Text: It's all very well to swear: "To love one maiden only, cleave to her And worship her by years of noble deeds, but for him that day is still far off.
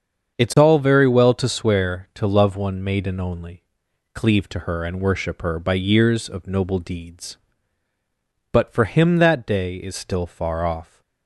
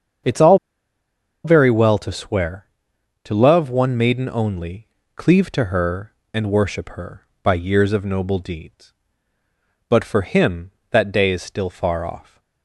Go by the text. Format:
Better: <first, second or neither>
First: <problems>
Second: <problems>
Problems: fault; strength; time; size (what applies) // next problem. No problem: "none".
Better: first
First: starts louder than the rest; until 1.4 s; 7 dB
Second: starts louder than the rest; strong; until 2.1 s; 7 dB // pauses between "all" and "very"; noticeable; at 0.5 s; 0.87 s long